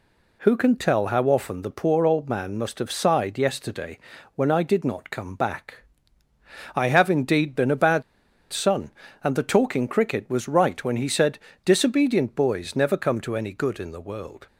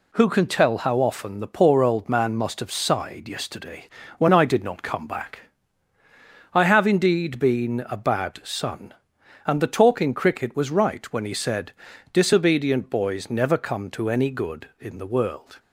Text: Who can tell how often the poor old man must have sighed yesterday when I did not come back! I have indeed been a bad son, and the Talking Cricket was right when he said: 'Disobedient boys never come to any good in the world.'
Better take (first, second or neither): second